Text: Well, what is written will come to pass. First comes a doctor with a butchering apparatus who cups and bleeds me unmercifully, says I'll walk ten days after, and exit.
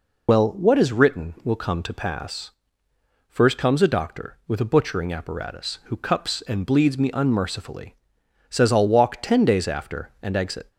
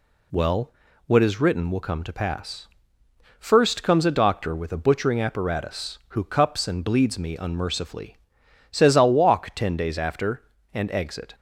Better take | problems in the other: second | loses the start of "Well"; at 0.2 s; 55 ms

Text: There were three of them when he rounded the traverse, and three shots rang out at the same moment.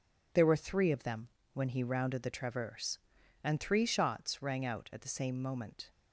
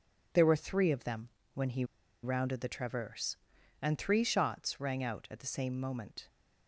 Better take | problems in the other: first | pauses between "them" and "when"; slight; at 1.2 s; 0.26 s long; slight in the first // pauses between "he" and "rounded"; at 1.8 s; 0.39 s long

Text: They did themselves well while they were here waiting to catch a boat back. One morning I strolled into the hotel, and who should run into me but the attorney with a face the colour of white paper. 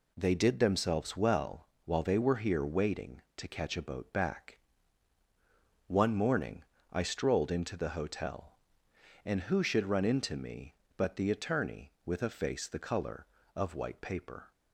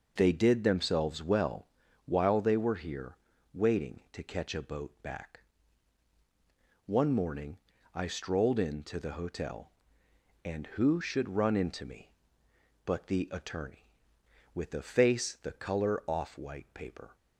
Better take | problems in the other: first | pauses between "well" and "while"; at 1.6 s; 0.40 s long; slight in the first // pauses between "here" and "waiting"; slight; at 3.1 s; 0.36 s long // pauses between "morning" and "I"; slight; at 7.5 s; 0.34 s long; slight in the first // says "off" for "of"; at 16.0 s

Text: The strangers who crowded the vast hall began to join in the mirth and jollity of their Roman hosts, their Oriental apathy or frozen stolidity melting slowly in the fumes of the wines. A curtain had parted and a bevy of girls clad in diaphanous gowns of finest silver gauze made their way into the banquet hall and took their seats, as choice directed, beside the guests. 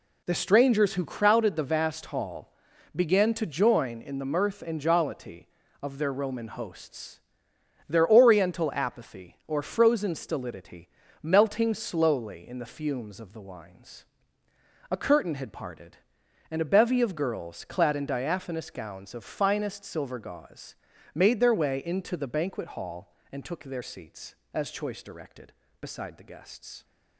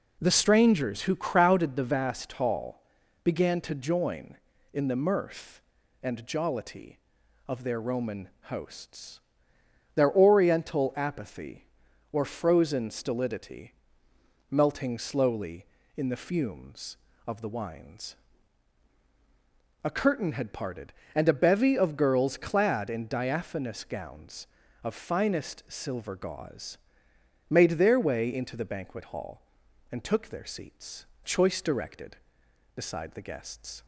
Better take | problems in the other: first | pauses between "hall" and "began"; at 2.8 s; 0.42 s long; also in the first // pauses between "Roman" and "hosts"; slight; at 8.2 s; 0.20 s long // pauses between "stolidity" and "melting"; noticeable; at 13.7 s; 0.80 s long; slight in the first // pauses between "gauze" and "made"; noticeable; at 26.7 s; 0.72 s long; slight in the first // skips "as"; at 31.1 s

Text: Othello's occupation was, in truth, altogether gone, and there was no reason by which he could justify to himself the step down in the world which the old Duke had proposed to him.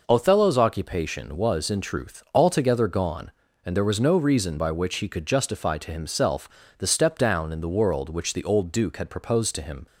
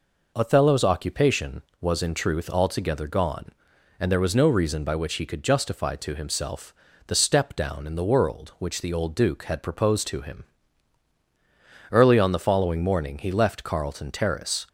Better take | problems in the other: first | pauses between "himself" and "the"; slight; at 6.7 s; 0.34 s long; slight in the first // goes on to say "Early on the following morning he left Carlton Terrace"; strong; from 11.9 s on; 2.7 s long

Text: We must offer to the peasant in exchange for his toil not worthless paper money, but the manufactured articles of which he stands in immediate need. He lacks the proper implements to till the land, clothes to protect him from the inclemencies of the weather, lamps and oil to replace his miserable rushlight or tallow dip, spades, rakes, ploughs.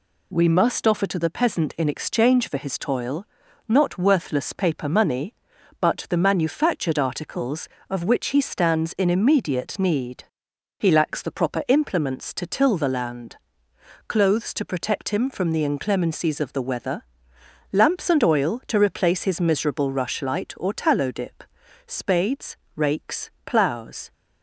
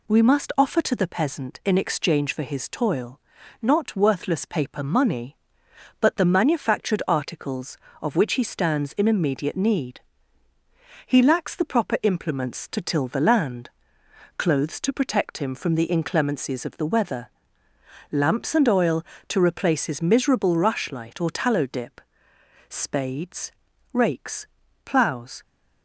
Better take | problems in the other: neither | pauses between "toil" and "not"; the same in both

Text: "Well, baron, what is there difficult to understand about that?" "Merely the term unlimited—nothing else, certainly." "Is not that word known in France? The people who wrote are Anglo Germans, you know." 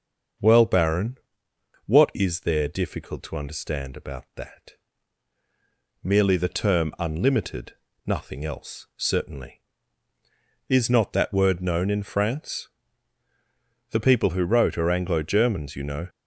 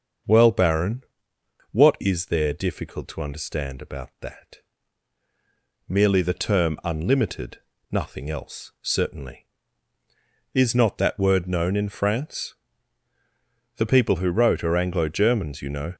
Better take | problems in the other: neither | starts louder than the rest; the same in both

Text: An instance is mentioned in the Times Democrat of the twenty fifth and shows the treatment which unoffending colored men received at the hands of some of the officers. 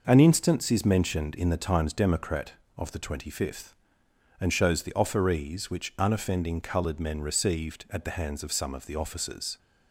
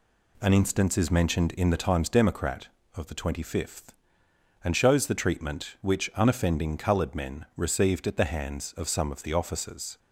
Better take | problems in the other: second | says "offerees" for "treatment"; at 4.9 s

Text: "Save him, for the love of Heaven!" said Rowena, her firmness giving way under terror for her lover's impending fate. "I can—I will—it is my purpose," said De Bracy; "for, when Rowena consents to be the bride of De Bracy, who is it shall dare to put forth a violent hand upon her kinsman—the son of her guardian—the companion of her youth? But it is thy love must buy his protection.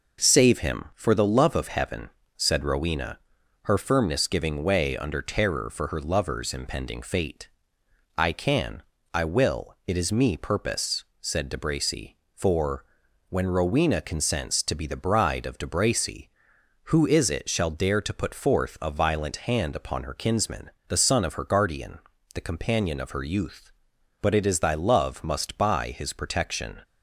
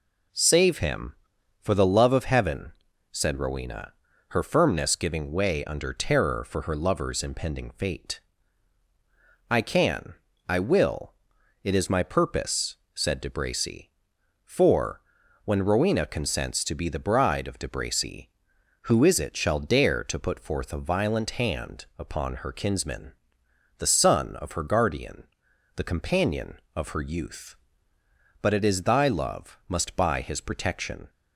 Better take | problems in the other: second | says "me" for "my"; at 10.1 s

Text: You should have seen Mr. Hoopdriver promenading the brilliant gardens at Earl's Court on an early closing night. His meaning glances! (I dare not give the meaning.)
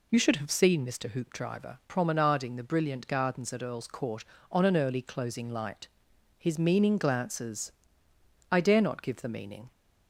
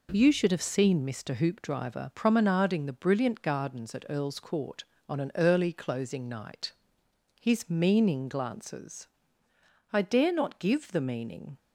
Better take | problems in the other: second | says "light" for "night"; at 5.4 s

